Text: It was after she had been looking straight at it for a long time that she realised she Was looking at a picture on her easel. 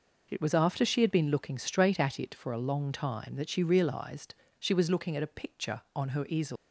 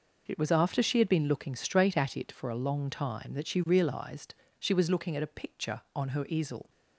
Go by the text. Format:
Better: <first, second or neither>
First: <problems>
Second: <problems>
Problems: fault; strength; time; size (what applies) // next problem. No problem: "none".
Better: second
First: pauses between "realised" and "she"; slight; at 4.3 s; 0.26 s long // leaves "easel" unfinished; at 6.5 s; 135 ms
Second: pauses between "realised" and "she"; slight; at 4.3 s; 0.26 s long